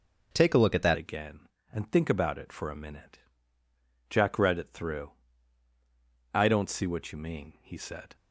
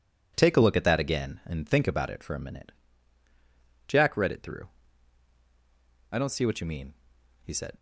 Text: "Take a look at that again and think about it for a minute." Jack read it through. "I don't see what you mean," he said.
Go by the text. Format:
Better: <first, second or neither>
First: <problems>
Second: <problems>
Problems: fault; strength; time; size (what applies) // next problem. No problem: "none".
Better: second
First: changes voice at "again"; from 0.9 s on; 7.2 s long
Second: none